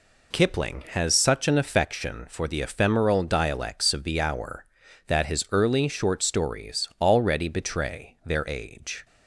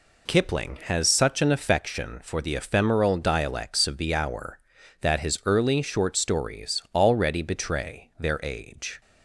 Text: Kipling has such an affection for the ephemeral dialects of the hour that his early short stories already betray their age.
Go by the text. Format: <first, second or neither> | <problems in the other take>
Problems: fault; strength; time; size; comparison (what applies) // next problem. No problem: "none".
neither | none